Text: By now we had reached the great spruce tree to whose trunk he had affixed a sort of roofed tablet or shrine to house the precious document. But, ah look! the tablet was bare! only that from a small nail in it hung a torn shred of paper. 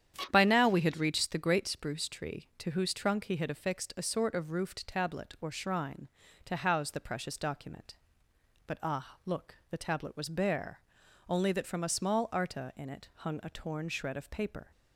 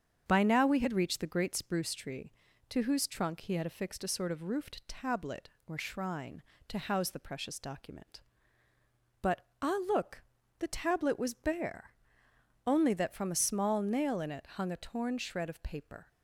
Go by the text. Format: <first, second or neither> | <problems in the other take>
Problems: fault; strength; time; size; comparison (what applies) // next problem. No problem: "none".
second | starts louder than the rest; strong; until 1.3 s; 9.5 dB; strong in the second // says "arta" for "nail"; at 12.3 s // pauses between "it" and "hung"; slight; at 13.0 s; 0.16 s long